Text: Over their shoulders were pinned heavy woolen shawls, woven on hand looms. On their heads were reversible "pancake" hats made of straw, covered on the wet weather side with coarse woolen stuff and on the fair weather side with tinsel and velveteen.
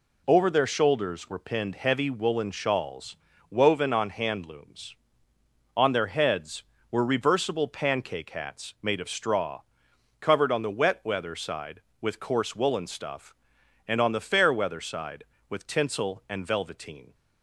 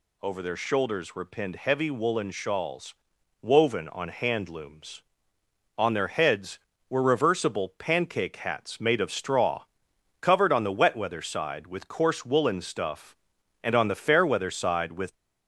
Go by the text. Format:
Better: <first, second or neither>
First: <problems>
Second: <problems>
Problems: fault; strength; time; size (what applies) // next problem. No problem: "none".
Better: first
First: none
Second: stops before "tinsel and velveteen"; at 15.1 s